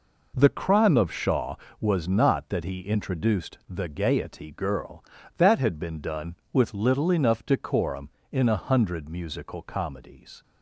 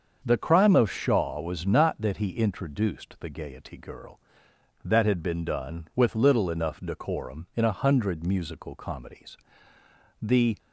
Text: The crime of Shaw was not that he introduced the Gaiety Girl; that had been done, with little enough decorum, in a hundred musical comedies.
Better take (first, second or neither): first